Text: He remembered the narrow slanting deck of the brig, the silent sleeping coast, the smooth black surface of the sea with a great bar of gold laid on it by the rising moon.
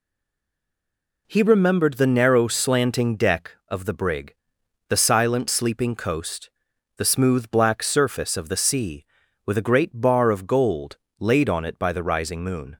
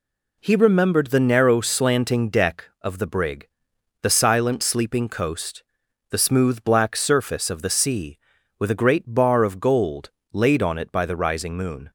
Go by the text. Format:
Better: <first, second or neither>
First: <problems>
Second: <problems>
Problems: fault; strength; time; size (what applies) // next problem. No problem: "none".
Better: second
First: stays silent before the first word; noticeable; until 1.2 s; 1.2 s long // pauses between "gold" and "laid"; slight; at 10.9 s; 0.22 s long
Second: pauses between "gold" and "laid"; slight; at 10.1 s; 0.22 s long